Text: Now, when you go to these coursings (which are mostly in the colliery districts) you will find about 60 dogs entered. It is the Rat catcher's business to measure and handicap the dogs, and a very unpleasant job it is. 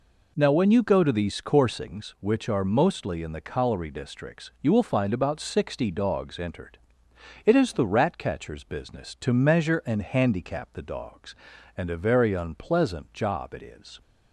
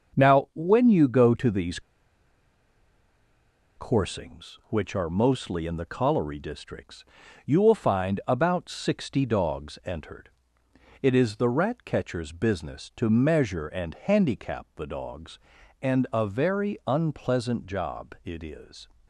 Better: first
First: none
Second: starts louder than the rest; until 1.2 s; 7 dB // pauses between "these" and "coursings"; strong; at 1.8 s; 1.9 s long

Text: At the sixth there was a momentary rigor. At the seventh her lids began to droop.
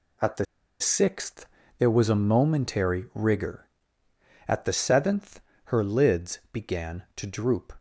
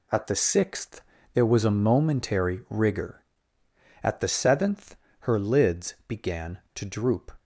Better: second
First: pauses between "the" and "sixth"; slight; at 0.4 s; 0.35 s long // pauses between "sixth" and "there"; slight; at 1.4 s; 0.34 s long // pauses between "seventh" and "her"; slight; at 5.3 s; 0.26 s long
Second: pauses between "sixth" and "there"; slight; at 1.0 s; 0.34 s long // pauses between "seventh" and "her"; slight; at 4.9 s; 0.26 s long

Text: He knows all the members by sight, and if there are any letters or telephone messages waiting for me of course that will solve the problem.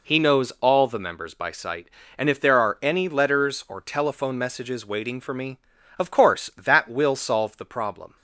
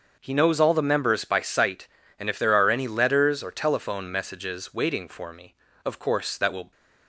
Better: first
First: none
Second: starts louder than the rest; until 1.1 s; 6.5 dB // stops before "solve the problem"; at 6.7 s

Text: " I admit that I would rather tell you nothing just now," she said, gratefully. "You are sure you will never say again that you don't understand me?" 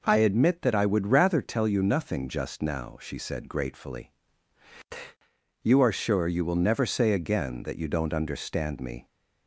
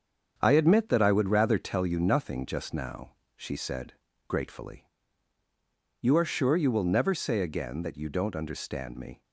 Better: first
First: none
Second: gets quieter; noticeable; throughout; 6 dB

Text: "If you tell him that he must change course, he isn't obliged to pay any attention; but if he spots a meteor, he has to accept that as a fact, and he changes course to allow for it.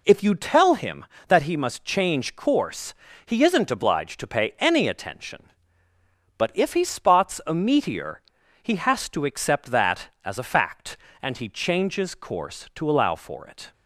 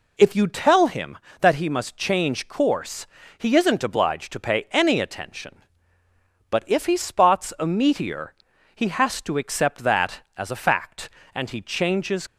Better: first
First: none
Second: stops before "course to allow for it"; at 12.2 s

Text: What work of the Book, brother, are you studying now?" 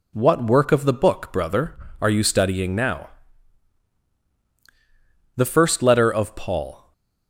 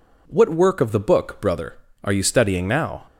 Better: second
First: goes on to say "The first letter of Paul"; from 5.3 s on; 1.5 s long // stays silent after the last word; slight; from 6.7 s on; 0.5 s long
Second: none

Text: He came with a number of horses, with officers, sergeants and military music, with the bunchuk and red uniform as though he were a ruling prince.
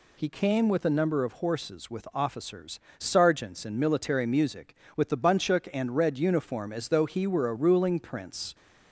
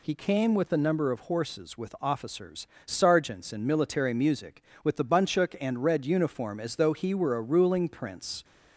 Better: neither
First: none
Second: none

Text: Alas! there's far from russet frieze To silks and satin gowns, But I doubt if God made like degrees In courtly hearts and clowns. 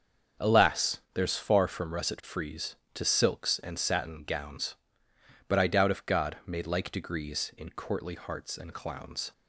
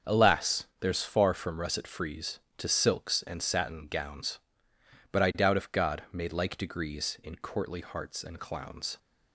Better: neither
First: starts louder than the rest; strong; until 1.5 s; 7 dB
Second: starts louder than the rest; strong; until 1.2 s; 7 dB

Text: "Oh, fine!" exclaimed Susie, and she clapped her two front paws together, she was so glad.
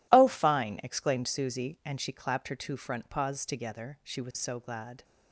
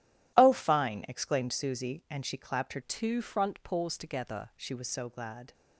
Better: first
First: none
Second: starts louder than the rest; strong; until 1.3 s; 12.5 dB // changes voice from "two" to "together"; from 2.8 to 4.5 s; 1.7 s long

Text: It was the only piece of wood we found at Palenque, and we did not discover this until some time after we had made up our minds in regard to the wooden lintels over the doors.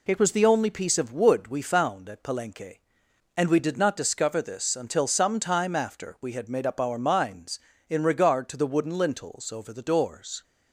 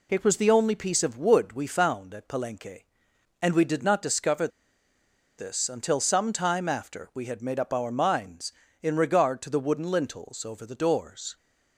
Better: first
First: none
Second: pauses between "discover" and "this"; noticeable; at 4.4 s; 0.89 s long

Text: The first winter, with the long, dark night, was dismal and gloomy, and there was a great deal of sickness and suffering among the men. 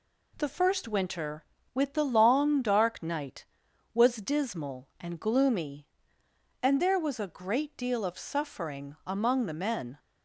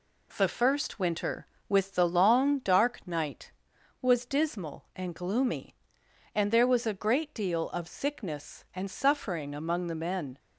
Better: second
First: skips "sickness and"; at 8.1 s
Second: none

